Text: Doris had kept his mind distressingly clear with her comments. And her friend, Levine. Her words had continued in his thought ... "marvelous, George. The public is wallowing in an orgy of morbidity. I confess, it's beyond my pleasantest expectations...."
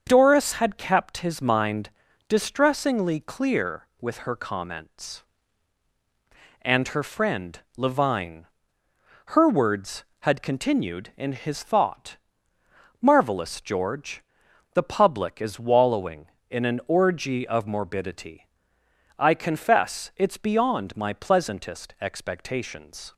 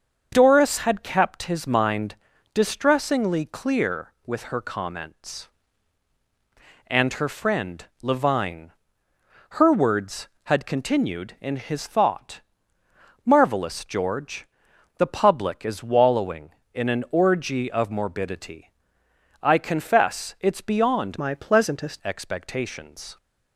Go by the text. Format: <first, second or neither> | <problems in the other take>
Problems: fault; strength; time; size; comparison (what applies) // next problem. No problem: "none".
first | starts louder than the rest; until 1.3 s; 6.5 dB; also in the first // pauses between "mind" and "distressingly"; at 2.1 s; 0.40 s long; also in the first // changes voice from "my" to "pleasantest"; from 21.1 to 21.9 s; 0.8 s long